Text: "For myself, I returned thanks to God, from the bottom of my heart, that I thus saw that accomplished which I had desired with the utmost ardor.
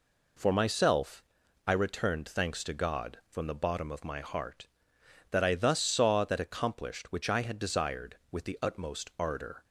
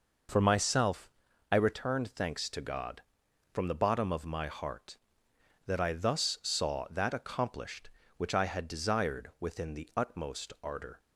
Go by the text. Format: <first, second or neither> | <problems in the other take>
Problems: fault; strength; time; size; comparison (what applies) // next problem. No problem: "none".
first | says "within" for "with"; at 9.3 s